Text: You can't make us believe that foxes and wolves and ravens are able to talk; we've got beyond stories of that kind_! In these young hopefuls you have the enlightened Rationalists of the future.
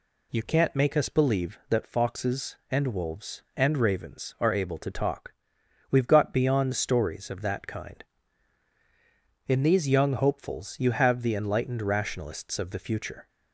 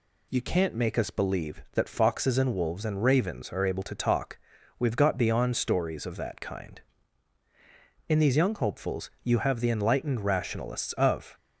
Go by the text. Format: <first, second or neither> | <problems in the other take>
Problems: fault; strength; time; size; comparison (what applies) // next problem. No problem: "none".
first | stops before "the future"; at 11.3 s